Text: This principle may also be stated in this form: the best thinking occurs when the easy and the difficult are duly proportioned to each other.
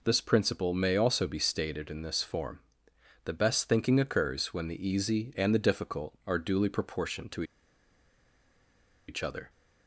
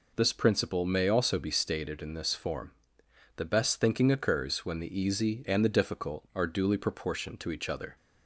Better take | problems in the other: second | pauses between "to" and "each"; strong; at 7.4 s; 1.6 s long

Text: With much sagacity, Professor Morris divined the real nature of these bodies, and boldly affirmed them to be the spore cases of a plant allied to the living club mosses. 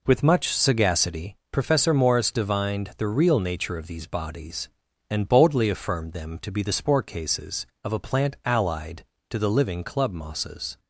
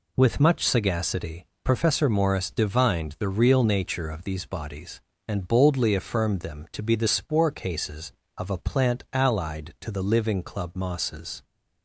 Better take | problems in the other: neither | none

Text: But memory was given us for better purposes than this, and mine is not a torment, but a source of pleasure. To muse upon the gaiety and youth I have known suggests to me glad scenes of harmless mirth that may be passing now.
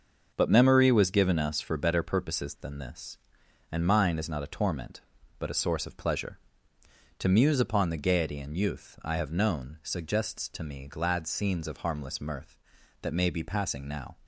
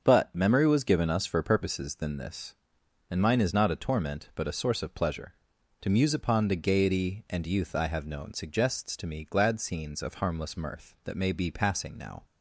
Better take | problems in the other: first | starts louder than the rest; until 1.0 s; 6.5 dB; also in the first // skips "better"; at 1.4 s

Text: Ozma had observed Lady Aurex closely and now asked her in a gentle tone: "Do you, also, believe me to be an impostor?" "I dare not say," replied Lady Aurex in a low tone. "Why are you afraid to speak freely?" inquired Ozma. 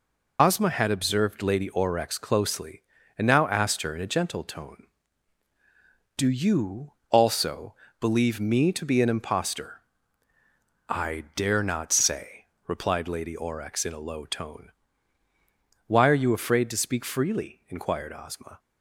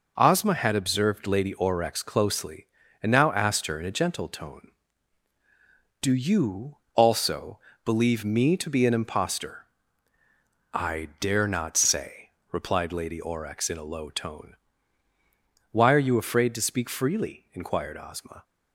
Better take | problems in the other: second | loses the start of "Ozma"; at 0.3 s; 70 ms

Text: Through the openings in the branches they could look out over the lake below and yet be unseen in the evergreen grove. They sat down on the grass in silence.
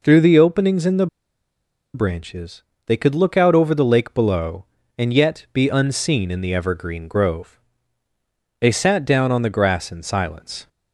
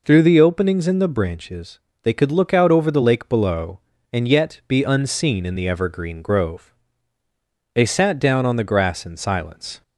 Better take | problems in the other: second | pauses between "the" and "branches"; noticeable; at 1.0 s; 0.87 s long // pauses between "branches" and "they"; slight; at 2.6 s; 0.24 s long; slight in the second

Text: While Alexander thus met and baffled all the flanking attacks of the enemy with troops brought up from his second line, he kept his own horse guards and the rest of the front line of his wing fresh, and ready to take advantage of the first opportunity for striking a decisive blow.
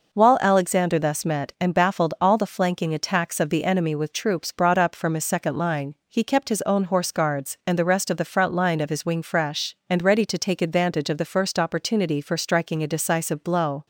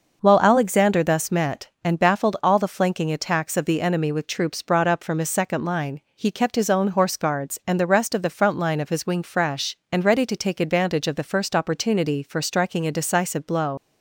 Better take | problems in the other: first | leaves "blow" unfinished; at 13.7 s; 90 ms

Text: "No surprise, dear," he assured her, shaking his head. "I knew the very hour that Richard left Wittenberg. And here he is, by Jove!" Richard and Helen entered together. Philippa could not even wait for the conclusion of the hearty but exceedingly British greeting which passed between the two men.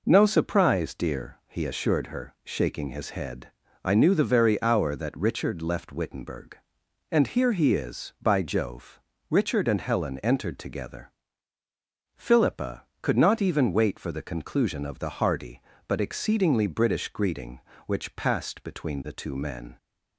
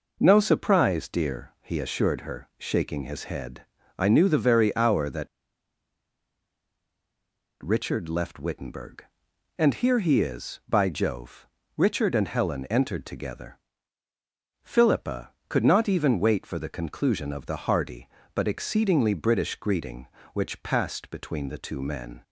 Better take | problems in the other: first | pauses between "that" and "Richard"; strong; at 5.2 s; 2.3 s long

